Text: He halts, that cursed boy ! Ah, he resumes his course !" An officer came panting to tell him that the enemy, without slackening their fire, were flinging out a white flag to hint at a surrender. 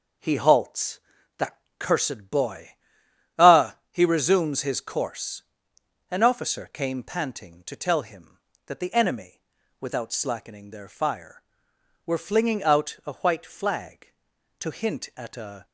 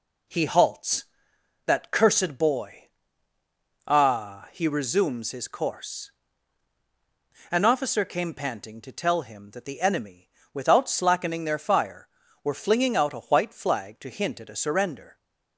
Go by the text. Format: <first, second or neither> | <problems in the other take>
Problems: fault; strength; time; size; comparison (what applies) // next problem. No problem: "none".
second | pauses between "that" and "cursed"; slight; at 1.5 s; 0.22 s long // stops before "surrender"; at 15.6 s